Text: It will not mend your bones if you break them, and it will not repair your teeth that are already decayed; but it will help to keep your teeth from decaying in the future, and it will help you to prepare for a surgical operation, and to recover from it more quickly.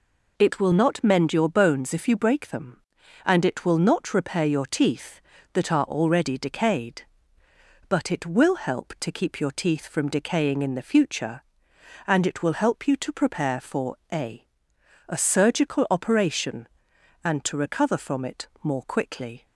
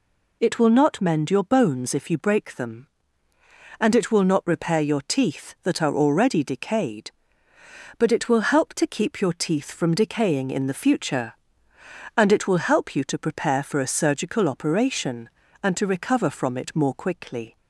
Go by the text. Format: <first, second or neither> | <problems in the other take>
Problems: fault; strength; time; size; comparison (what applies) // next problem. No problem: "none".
second | pauses between "for" and "a"; slight; at 13.9 s; 0.16 s long // says "a" twice; at 15.0 s